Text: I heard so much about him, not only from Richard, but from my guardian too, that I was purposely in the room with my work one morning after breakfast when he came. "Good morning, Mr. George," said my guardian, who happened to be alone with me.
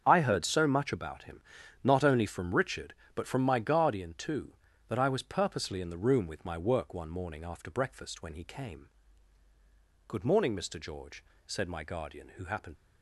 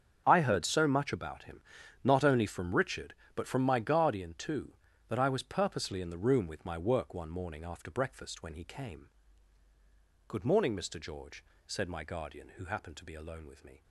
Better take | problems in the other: second | starts louder than the rest; strong; until 1.0 s; 7.5 dB; strong in the second // stops before "to be alone with me"; at 12.7 s

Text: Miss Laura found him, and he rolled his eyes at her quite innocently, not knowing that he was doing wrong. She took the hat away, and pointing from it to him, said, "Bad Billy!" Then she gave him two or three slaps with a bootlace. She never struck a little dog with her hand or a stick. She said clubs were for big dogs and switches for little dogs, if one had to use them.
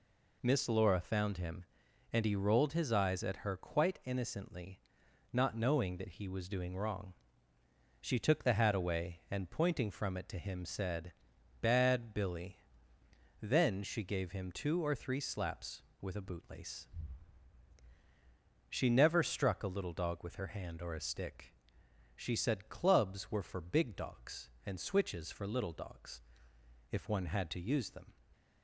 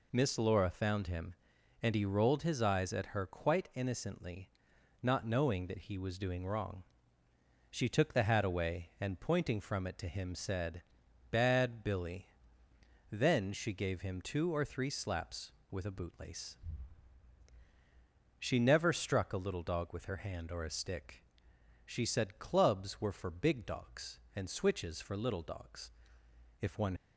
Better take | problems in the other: first | stops before "had to use them"; at 26.9 s

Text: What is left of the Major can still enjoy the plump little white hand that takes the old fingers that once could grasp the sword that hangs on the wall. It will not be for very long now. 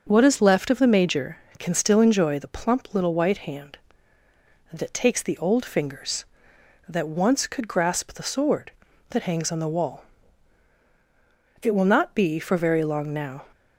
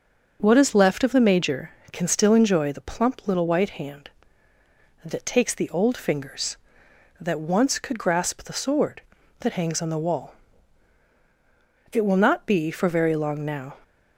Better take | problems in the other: neither | starts louder than the rest; the same in both

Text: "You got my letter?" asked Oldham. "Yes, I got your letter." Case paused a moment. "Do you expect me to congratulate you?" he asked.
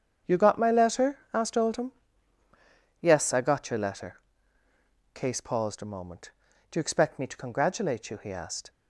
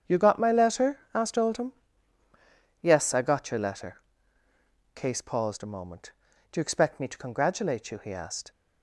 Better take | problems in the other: neither | starts louder than the rest; strong; the same in both

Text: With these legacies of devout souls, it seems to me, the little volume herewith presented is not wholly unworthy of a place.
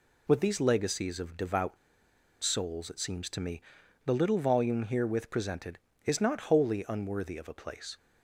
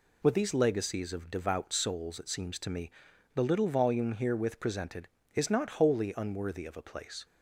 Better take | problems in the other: second | pauses between "devout" and "souls"; noticeable; at 1.7 s; 0.65 s long

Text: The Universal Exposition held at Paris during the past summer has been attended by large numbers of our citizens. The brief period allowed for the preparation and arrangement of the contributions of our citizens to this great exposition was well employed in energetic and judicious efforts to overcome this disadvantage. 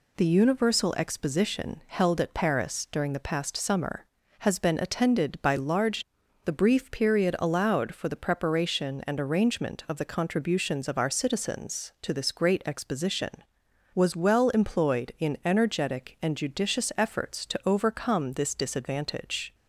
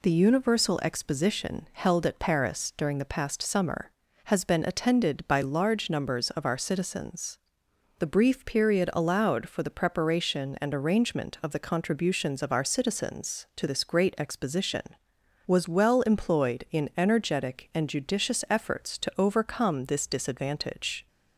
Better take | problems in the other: second | skips "numbers of our citizens"; at 6.2 s

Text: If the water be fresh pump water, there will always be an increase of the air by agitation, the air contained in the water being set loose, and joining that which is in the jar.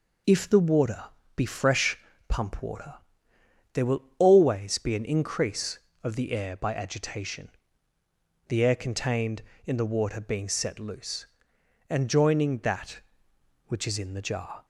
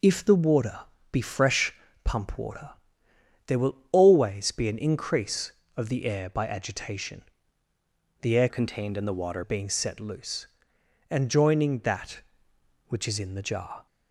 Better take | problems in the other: first | pauses between "water" and "be"; slight; at 0.8 s; 0.32 s long; slight in the first // pauses between "fresh" and "pump"; slight; at 1.7 s; 0.30 s long; slight in the first // pauses between "will" and "always"; slight; at 3.7 s; 0.16 s long; slight in the first // changes voice from "contained" to "water"; from 8.4 to 9.4 s; 1.0 s long

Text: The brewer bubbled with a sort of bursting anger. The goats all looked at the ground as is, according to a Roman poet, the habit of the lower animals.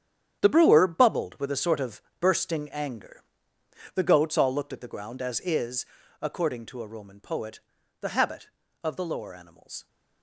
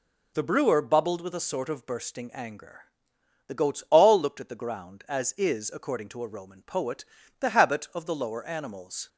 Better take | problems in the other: second | gets quieter; strong; throughout; 11 dB // pauses between "of" and "bursting"; slight; at 2.0 s; 0.18 s long

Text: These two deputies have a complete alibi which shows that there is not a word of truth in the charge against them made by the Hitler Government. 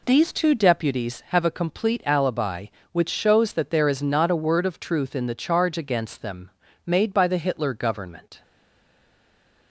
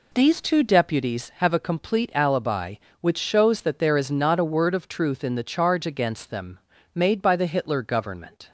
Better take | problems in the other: second | pauses between "them" and "made"; slight; at 6.5 s; 0.34 s long; slight in the second // stays silent after the last word; noticeable; from 8.4 s on; 1.3 s long

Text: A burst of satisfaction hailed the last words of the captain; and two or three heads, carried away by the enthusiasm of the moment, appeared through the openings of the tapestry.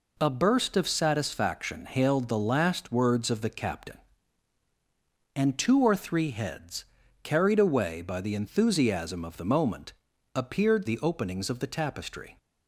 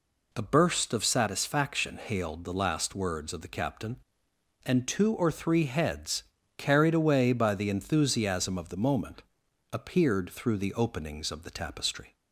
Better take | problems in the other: second | skips "through"; at 10.8 s

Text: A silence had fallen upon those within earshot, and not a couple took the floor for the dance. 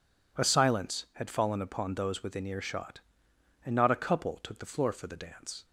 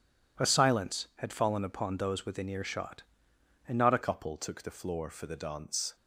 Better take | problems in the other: first | changes voice at "couple"; from 4.0 s on; 1.9 s long

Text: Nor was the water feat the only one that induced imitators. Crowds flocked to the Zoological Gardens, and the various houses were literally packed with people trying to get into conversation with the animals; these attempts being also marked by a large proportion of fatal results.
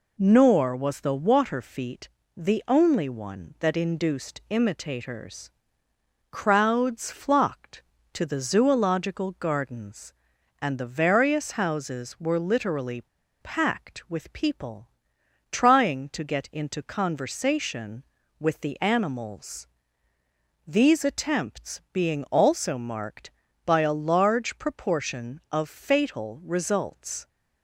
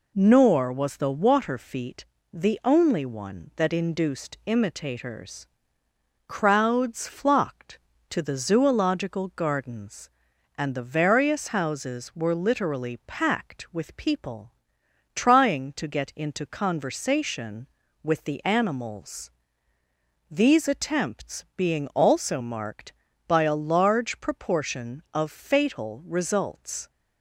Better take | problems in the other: second | pauses between "feat" and "the"; slight; at 2.0 s; 0.28 s long; slight in the second // pauses between "literally" and "packed"; at 13.0 s; 0.42 s long // pauses between "people" and "trying"; noticeable; at 14.8 s; 0.64 s long; noticeable in the second

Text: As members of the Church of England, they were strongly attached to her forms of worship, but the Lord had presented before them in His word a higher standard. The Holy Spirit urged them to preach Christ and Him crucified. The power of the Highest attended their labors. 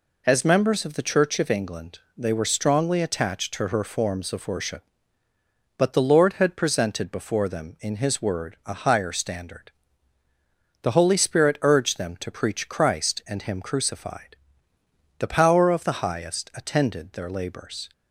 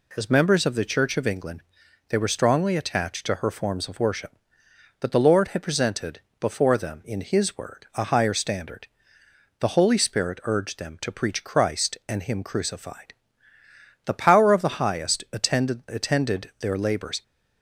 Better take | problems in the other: first | pauses between "presented" and "before"; slight; at 6.2 s; 0.20 s long // says "attended" twice; at 15.8 s

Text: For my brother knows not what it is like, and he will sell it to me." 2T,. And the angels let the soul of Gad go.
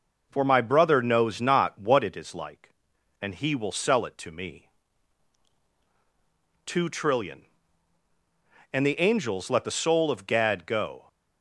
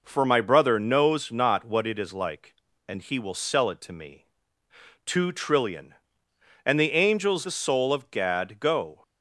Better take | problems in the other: first | skips "let"; at 7.4 s

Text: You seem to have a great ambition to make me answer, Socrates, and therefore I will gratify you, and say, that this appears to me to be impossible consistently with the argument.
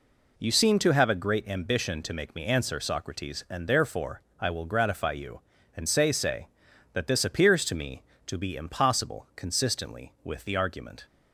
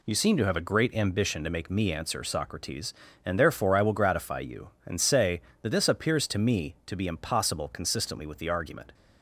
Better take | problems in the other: second | pauses between "therefore" and "I"; slight; at 4.1 s; 0.18 s long // says "say" twice; at 6.1 s

